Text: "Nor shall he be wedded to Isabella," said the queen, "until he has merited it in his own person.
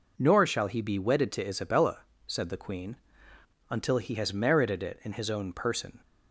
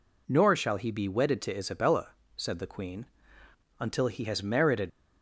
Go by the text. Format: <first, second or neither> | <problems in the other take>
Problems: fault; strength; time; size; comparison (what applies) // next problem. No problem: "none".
first | stops before "it in his own person"; at 4.8 s